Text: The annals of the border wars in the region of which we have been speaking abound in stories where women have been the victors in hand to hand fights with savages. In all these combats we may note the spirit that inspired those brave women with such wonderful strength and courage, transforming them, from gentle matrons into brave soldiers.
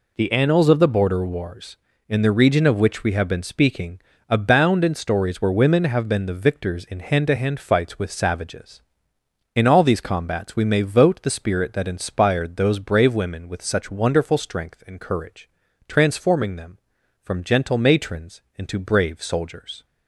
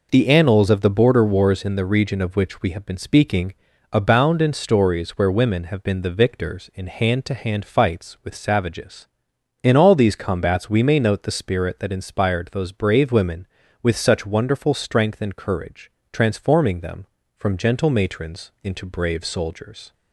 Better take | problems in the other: second | pauses between "speaking" and "abound"; slight; at 3.9 s; 0.30 s long; also in the second // says "vote" for "note"; at 10.8 s

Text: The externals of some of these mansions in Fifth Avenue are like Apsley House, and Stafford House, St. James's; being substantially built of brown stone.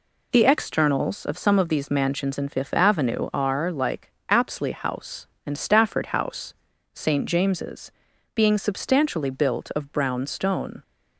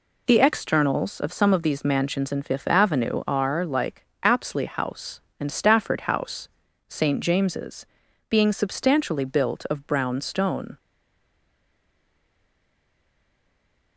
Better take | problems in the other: first | pauses between "like" and "Apsley"; slight; at 4.0 s; 0.18 s long; slight in the first // stays silent after the last word; strong; from 10.7 s on; 3.2 s long

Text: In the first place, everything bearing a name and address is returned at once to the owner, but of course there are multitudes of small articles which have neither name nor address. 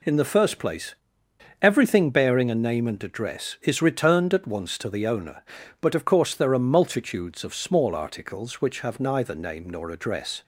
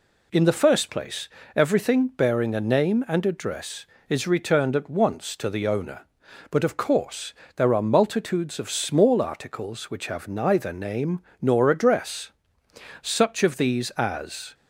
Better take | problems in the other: first | pauses between "course" and "there"; slight; at 7.3 s; 0.22 s long // pauses between "name" and "nor"; slight; at 11.1 s; 0.22 s long // goes on to say "Such of these as"; from 13.0 s on; 1.5 s long

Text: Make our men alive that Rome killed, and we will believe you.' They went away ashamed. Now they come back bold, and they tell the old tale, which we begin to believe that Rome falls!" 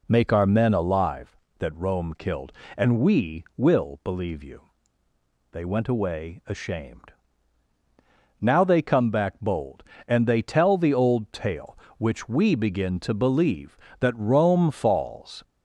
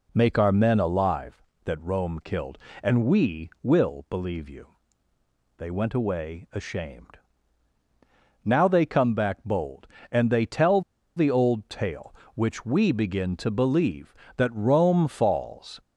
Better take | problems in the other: first | pauses between "tell" and "the"; slight; at 10.8 s; 0.35 s long

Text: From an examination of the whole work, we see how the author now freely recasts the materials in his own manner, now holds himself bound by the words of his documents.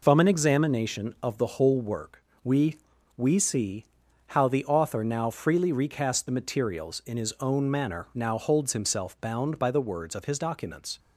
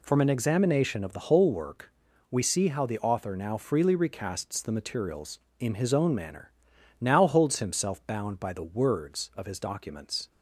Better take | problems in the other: second | says "we" twice; at 3.1 s // pauses between "see" and "how"; noticeable; at 3.8 s; 0.50 s long

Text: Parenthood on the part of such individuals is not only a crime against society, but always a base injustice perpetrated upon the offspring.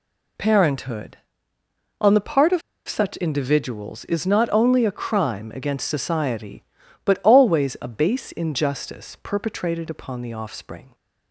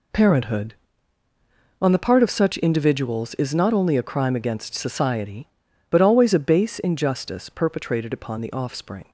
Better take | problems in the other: second | pauses between "of" and "such"; slight; at 2.6 s; 0.27 s long

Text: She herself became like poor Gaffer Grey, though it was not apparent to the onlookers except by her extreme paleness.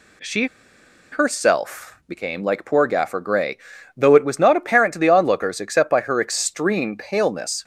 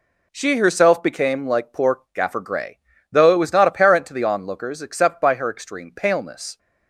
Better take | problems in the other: second | pauses between "She" and "herself"; noticeable; at 0.4 s; 0.65 s long

